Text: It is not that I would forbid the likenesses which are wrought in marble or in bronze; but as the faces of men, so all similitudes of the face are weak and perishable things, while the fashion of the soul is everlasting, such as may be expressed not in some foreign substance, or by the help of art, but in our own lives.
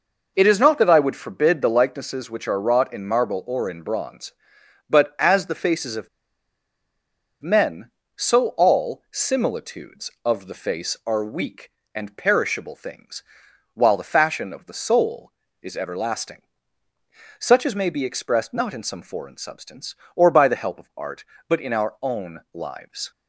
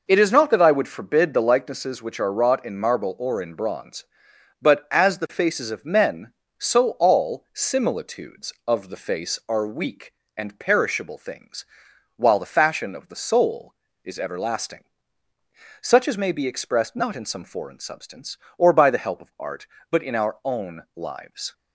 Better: second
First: pauses between "of" and "men"; strong; at 6.0 s; 1.3 s long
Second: none

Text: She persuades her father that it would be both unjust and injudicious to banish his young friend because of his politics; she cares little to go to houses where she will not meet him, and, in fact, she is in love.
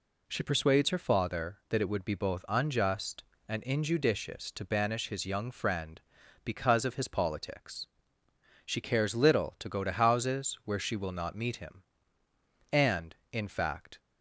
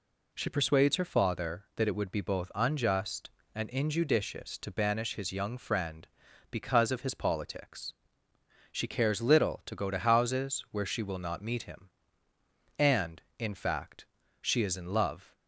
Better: second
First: stops before "she is in love"; at 13.9 s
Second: none

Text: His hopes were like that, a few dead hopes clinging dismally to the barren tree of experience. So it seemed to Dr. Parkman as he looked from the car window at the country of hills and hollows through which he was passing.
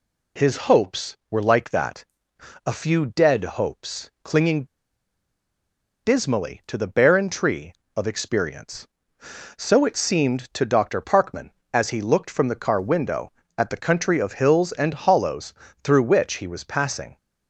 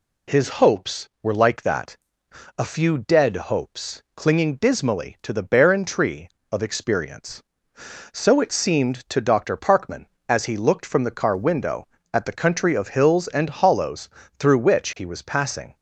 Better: second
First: pauses between "clinging" and "dismally"; strong; at 4.6 s; 1.3 s long // pauses between "hollows" and "through"; slight; at 15.5 s; 0.28 s long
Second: pauses between "hollows" and "through"; slight; at 14.1 s; 0.28 s long

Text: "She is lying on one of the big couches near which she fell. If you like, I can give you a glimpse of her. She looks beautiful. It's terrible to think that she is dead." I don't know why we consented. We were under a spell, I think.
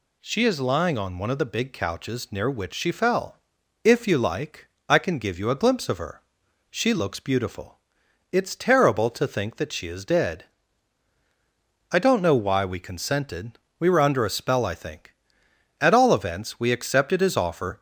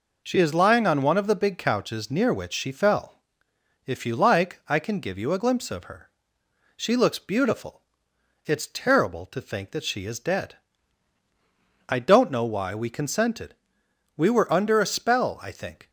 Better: second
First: goes on to say "At all events we accepted his offer"; strong; from 15.7 s on; 2.0 s long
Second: none

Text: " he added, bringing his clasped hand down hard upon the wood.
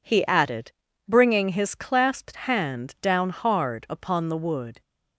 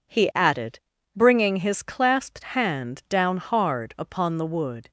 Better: neither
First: none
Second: none

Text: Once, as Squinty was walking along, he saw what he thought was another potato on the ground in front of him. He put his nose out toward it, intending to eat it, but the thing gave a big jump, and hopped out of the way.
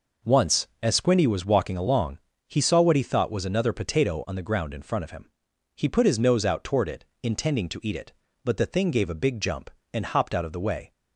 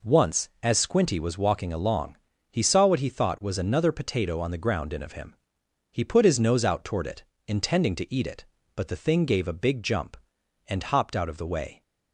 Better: first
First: none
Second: skips "front"; at 5.0 s

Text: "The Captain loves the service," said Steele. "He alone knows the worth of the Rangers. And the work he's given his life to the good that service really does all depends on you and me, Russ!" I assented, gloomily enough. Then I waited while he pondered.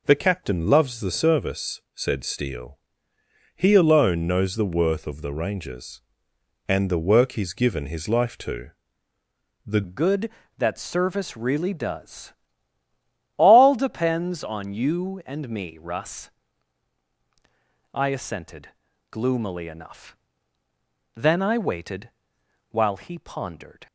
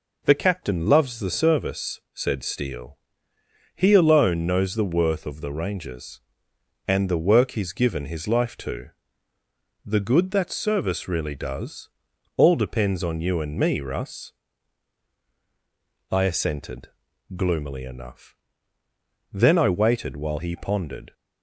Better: second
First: pauses between "to" and "the"; noticeable; at 8.6 s; 0.96 s long // changes voice at "good"; from 9.8 s on; 14.0 s long // pauses between "does" and "all"; at 12.3 s; 1.0 s long // pauses between "waited" and "while"; noticeable; at 22.1 s; 0.58 s long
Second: pauses between "to" and "the"; noticeable; at 8.8 s; 0.96 s long // pauses between "does" and "all"; noticeable; at 11.8 s; 0.46 s long

